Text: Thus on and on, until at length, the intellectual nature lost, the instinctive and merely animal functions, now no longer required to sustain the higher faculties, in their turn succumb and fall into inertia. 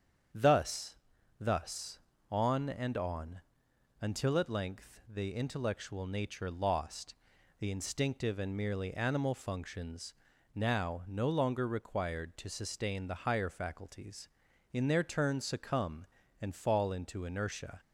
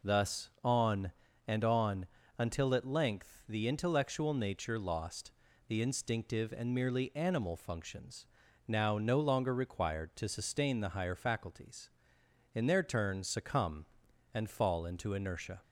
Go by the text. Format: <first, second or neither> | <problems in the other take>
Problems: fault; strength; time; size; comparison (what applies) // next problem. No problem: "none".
second | starts louder than the rest; strong; until 1.7 s; 8 dB // says "Thus" twice; at 1.3 s